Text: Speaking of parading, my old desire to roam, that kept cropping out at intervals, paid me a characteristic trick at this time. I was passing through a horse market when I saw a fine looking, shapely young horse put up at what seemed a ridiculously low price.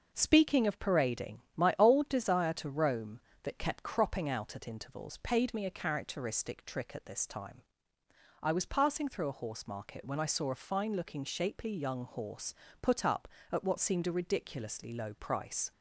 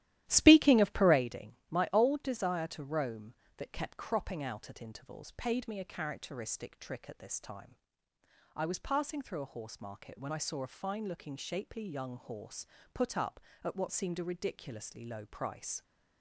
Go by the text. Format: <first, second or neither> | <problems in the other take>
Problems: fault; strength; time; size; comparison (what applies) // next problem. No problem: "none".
first | starts louder than the rest; strong; until 1.2 s; 13.5 dB // pauses between "horse" and "put"; slight; at 12.6 s; 0.30 s long; slight in the first